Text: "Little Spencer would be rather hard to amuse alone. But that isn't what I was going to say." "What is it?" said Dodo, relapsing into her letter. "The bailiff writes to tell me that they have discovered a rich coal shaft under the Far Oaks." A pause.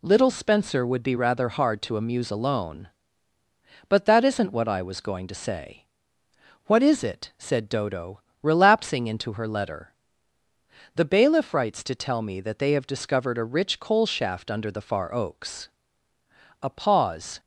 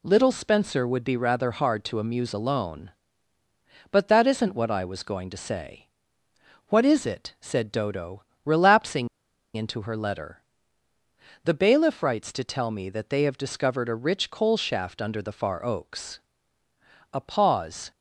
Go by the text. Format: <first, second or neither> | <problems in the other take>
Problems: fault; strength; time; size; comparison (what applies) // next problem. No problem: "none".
first | pauses between "relapsing" and "into"; noticeable; at 9.0 s; 0.48 s long